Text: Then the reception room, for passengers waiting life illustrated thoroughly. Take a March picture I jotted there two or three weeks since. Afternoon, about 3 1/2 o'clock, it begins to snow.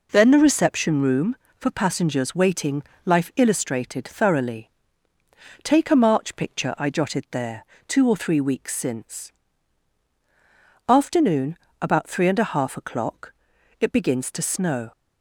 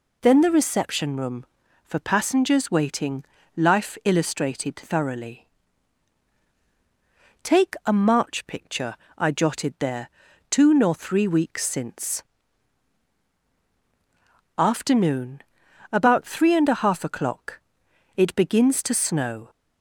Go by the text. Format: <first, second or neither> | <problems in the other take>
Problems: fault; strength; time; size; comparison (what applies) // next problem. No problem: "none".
first | pauses between "waiting" and "life"; slight; at 3.2 s; 0.32 s long; slight in the first // pauses between "picture" and "I"; slight; at 8.9 s; 0.22 s long // pauses between "there" and "two"; at 10.0 s; 0.40 s long; slight in the first // says "nor" for "or"; at 10.7 s